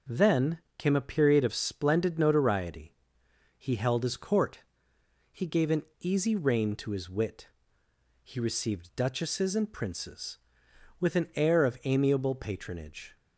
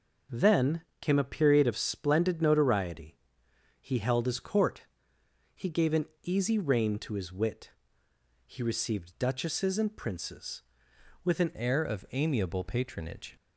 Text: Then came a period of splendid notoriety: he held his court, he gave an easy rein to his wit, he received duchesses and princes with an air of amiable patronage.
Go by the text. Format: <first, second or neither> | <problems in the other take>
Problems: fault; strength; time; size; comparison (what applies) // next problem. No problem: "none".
first | pauses between "Then" and "came"; slight; at 0.8 s; 0.18 s long; slight in the first // pauses between "an" and "easy"; slight; at 6.0 s; 0.16 s long; slight in the first // changes voice at "air"; from 11.5 s on; 1.8 s long